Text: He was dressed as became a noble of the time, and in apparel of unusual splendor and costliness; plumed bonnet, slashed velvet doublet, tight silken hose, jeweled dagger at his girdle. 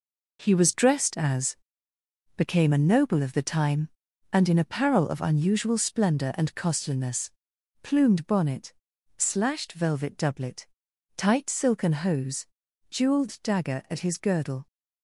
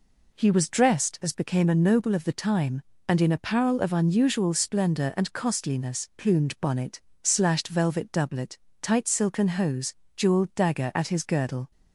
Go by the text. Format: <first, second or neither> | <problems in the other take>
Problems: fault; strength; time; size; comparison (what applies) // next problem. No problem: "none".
second | gets quieter; throughout; 7 dB // pauses between "as" and "became"; noticeable; at 1.5 s; 0.82 s long